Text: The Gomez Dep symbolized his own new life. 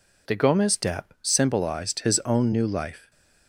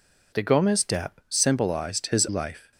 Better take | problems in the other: first | skips "own new"; at 2.2 s

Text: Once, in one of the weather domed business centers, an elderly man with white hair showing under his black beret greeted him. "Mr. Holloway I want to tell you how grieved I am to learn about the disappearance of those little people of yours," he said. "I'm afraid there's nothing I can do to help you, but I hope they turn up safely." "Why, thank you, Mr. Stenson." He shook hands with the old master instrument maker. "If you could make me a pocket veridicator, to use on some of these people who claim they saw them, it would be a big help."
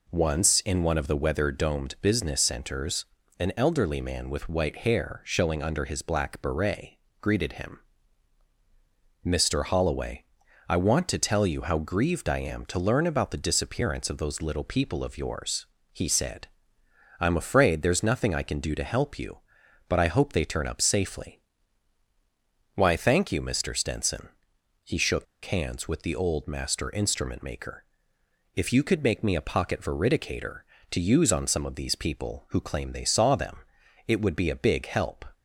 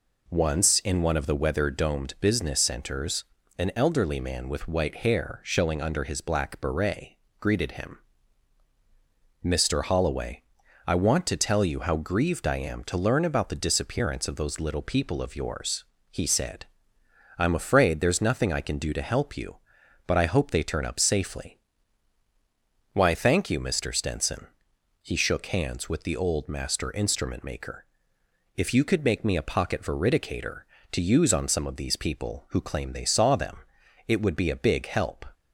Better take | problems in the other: second | pauses between "beret" and "greeted"; slight; at 6.9 s; 0.24 s long; slight in the second // pauses between "Holloway" and "I"; noticeable; at 10.2 s; 0.46 s long; noticeable in the second // pauses between "shook" and "hands"; slight; at 25.2 s; 0.20 s long

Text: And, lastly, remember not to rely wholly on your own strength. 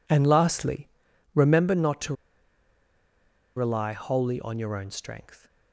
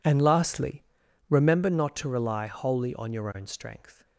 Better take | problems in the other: second | pauses between "to" and "rely"; strong; at 2.1 s; 1.4 s long

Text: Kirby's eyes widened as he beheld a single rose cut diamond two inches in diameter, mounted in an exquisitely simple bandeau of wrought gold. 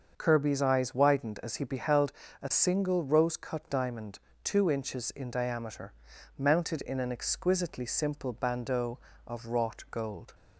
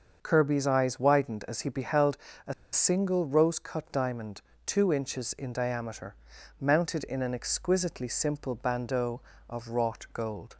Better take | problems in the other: first | starts louder than the rest; until 1.2 s; 6.5 dB; also in the first // pauses between "beheld" and "a"; slight; at 2.1 s; 0.28 s long; slight in the first // pauses between "a" and "single"; slight; at 2.5 s; 0.19 s long // pauses between "diamond" and "two"; slight; at 4.4 s; 0.24 s long; slight in the first

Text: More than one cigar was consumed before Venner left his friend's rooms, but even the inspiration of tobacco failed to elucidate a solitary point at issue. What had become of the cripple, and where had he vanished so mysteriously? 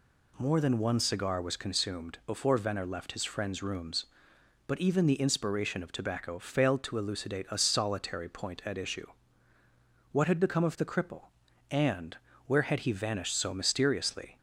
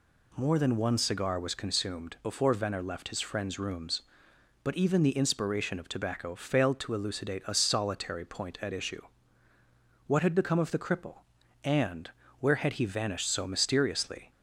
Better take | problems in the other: neither | pauses between "and" and "where"; slight; the same in both

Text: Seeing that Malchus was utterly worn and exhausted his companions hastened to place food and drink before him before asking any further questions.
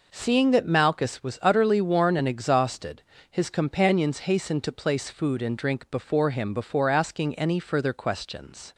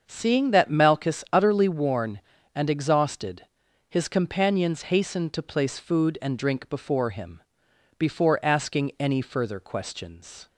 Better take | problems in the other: first | starts louder than the rest; until 1.0 s; 6.5 dB // skips "was"; at 1.2 s // pauses between "exhausted" and "his"; at 3.4 s; 0.42 s long; slight in the first // pauses between "him" and "before"; noticeable; at 7.4 s; 0.56 s long

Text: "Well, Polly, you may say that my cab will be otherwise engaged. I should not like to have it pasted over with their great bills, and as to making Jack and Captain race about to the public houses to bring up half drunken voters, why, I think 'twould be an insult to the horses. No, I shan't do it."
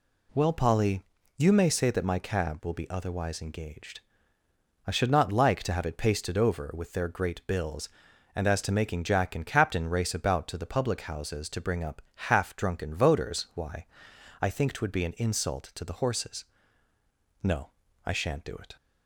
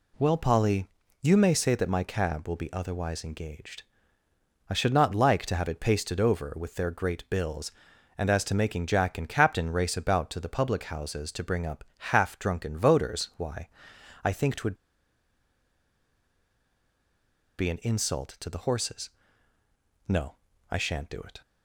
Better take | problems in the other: first | pauses between "twould" and "be"; strong; at 14.7 s; 2.8 s long

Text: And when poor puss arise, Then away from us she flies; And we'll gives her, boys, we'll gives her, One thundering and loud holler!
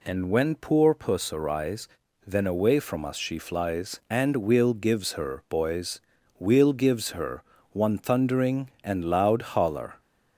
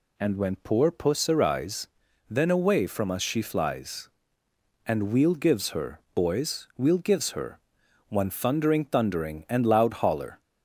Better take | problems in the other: first | says "thundering" twice; at 8.8 s

